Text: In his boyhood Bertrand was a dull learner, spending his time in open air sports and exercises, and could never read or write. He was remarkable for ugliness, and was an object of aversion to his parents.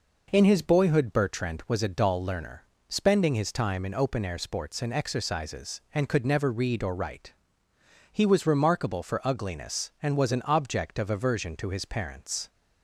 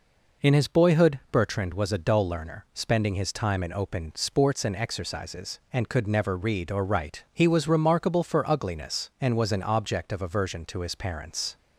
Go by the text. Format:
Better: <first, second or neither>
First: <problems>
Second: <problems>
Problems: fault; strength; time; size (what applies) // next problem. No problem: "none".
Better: first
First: none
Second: skips "air"; at 4.1 s